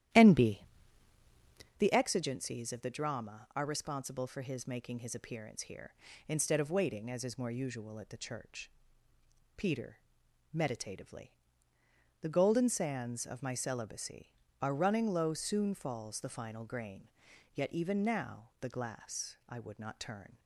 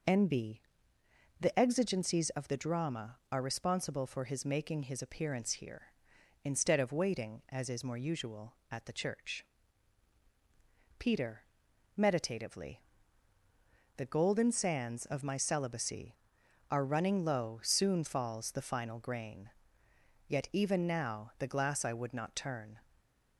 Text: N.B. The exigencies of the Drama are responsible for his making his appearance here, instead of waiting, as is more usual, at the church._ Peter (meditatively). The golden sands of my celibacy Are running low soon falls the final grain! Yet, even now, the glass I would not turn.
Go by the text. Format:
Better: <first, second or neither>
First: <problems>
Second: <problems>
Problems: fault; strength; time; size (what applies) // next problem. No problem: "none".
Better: second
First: starts louder than the rest; strong; until 1.9 s; 12 dB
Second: none